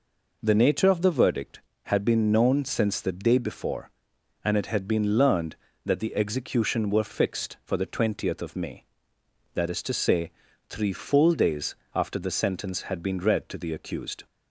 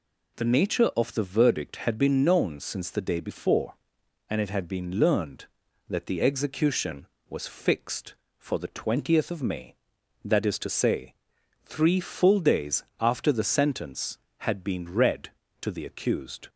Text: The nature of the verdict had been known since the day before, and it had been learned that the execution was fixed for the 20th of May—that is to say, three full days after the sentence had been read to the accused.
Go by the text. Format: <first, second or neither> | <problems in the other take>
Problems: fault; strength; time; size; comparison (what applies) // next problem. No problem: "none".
second | says "were" for "was"; at 6.9 s // pauses between "days" and "after"; slight; at 11.7 s; 0.20 s long; slight in the second